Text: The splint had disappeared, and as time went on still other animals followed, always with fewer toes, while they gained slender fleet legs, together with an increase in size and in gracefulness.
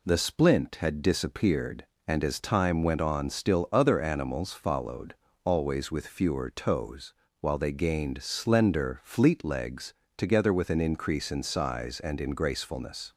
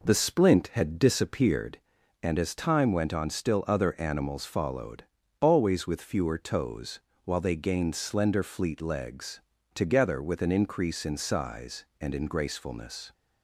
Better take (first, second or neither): first